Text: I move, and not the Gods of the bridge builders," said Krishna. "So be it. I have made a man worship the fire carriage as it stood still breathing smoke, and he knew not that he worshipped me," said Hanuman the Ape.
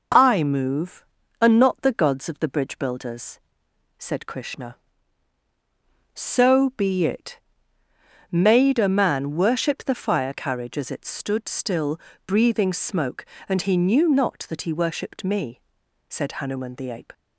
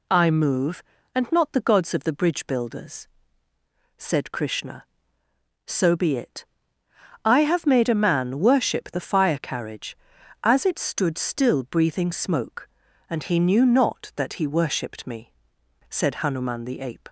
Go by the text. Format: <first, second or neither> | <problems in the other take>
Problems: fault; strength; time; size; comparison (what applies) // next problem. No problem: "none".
second | skips "I have"; at 7.8 s // pauses between "still" and "breathing"; slight; at 11.9 s; 0.28 s long